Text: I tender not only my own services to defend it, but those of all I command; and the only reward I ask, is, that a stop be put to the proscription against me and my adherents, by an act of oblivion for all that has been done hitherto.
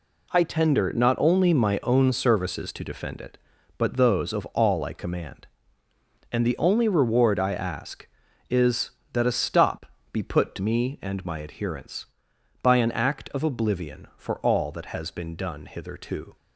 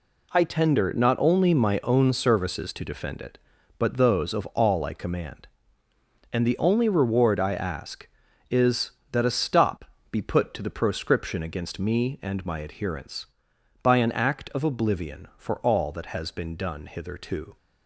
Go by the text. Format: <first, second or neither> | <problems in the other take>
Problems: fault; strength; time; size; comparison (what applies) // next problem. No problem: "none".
second | pauses between "stop" and "be"; slight; at 9.8 s; 0.24 s long; slight in the second // skips "the proscription against"; at 10.5 s